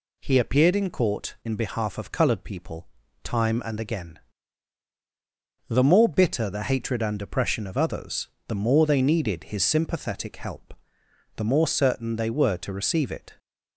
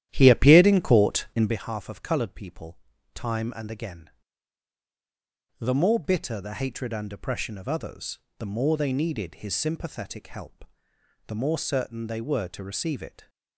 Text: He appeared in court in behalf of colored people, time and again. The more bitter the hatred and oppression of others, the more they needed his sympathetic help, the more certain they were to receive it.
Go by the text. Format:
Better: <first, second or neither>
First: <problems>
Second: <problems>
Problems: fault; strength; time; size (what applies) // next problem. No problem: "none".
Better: first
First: none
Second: starts louder than the rest; strong; until 1.6 s; 12 dB